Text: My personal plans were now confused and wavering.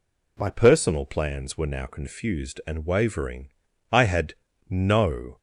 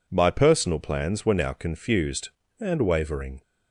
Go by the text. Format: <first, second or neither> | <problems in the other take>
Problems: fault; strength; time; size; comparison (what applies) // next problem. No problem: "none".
second | goes on to say "I had no"; from 3.8 s on; 1.4 s long